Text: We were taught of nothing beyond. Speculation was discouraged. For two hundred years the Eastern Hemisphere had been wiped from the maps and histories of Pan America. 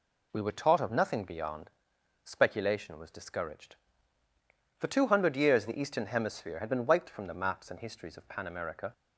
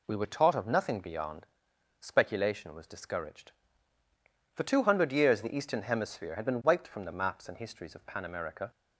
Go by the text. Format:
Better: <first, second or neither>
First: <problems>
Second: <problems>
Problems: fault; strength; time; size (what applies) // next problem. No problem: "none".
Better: neither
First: none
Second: none